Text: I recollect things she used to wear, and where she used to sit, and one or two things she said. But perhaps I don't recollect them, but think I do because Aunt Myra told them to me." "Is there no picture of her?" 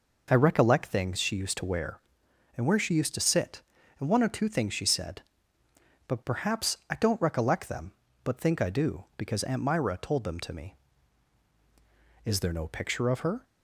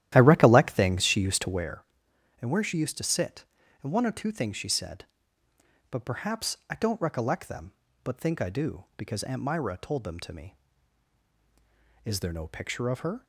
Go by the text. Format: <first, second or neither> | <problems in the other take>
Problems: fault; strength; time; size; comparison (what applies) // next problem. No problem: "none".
first | starts louder than the rest; strong; until 1.7 s; 12.5 dB